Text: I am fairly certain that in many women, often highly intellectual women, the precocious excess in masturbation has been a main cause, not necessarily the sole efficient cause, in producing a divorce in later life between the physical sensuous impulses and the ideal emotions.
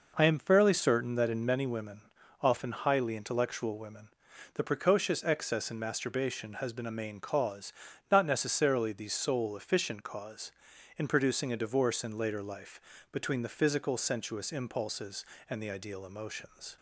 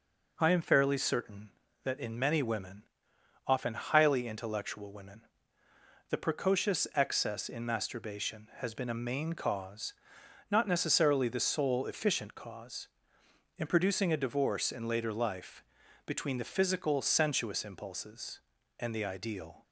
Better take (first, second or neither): first